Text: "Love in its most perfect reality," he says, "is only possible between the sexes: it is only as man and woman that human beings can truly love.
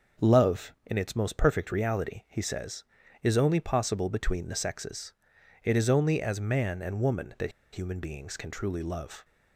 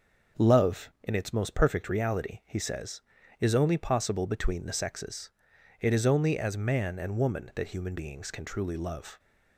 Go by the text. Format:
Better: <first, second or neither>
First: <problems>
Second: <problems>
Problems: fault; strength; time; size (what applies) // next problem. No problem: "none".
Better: second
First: starts louder than the rest; until 1.3 s; 6.5 dB // pauses between "that" and "human"; slight; at 7.4 s; 0.22 s long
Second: starts louder than the rest; until 1.5 s; 6.5 dB